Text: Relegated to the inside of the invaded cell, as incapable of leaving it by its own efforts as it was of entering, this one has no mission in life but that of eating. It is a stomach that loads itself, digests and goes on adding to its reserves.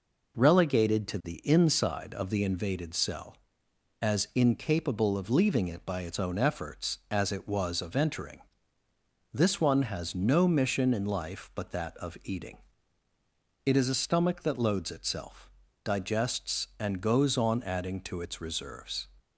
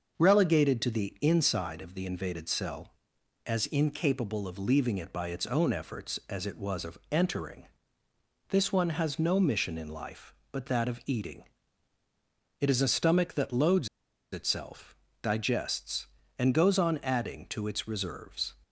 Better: first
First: none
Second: starts louder than the rest; noticeable; until 1.2 s; 6 dB // pauses between "loads" and "itself"; at 13.8 s; 0.45 s long

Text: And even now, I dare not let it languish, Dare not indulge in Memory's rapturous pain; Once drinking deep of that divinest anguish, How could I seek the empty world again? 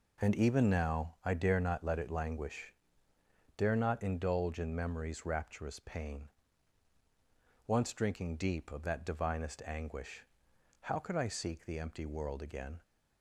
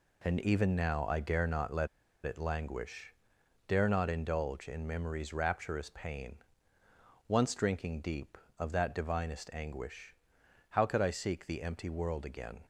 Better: first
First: none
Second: pauses between "let" and "it"; at 1.8 s; 0.38 s long

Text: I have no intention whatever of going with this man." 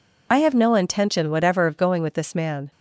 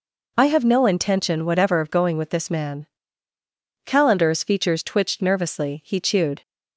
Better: first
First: none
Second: goes on to say "Calendar's features twitched nervously he chewed"; strong; from 3.8 s on; 2.5 s long

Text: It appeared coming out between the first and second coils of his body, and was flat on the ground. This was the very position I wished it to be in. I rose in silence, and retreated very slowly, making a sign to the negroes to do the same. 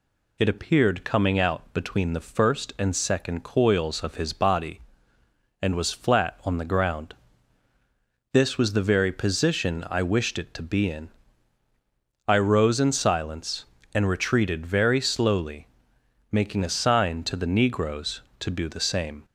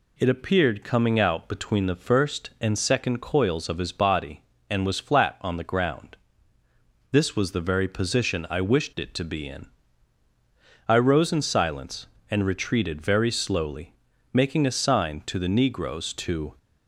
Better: first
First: none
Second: stops before "do the same"; at 16.5 s

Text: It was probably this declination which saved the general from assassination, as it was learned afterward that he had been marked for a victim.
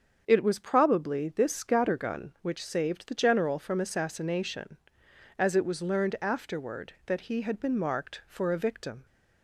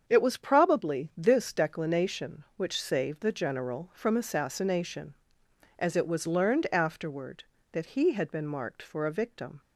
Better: second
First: starts louder than the rest; until 1.2 s; 7 dB // says "scattergun" for "declination"; at 1.5 s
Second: starts louder than the rest; strong; until 1.0 s; 7.5 dB

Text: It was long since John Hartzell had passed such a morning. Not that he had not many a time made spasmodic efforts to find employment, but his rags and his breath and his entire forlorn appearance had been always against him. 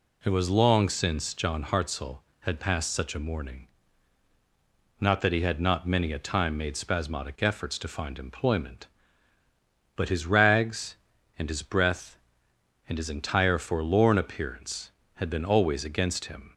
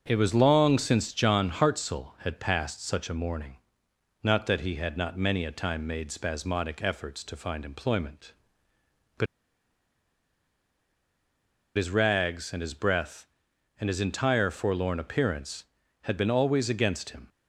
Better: first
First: none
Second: starts louder than the rest; until 1.0 s; 6 dB // pauses between "but" and "his"; strong; at 9.2 s; 2.5 s long

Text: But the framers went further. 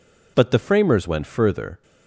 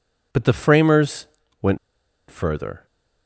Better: first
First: none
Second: pauses between "framers" and "went"; slight; at 1.2 s; 0.34 s long // pauses between "went" and "further"; noticeable; at 1.7 s; 0.53 s long

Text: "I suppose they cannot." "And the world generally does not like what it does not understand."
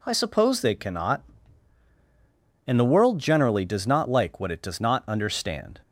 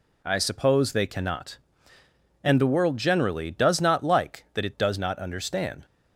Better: first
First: none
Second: says "that" for "what"; at 4.5 s

